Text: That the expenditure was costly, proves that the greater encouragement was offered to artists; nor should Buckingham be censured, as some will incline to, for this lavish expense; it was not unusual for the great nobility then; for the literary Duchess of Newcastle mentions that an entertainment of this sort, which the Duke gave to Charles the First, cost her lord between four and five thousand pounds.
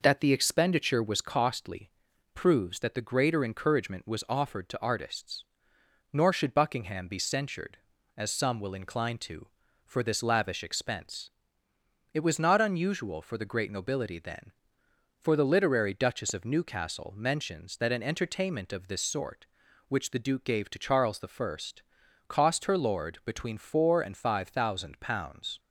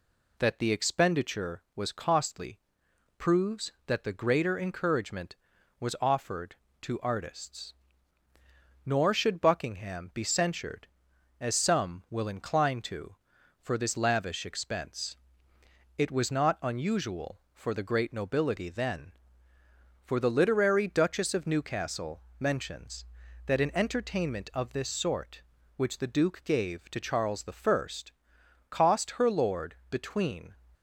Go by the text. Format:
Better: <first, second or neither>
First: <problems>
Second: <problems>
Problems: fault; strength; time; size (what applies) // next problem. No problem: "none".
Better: first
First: none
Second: pauses between "Newcastle" and "mentions"; slight; at 22.2 s; 0.18 s long // stops before "four and five thousand pounds"; at 30.7 s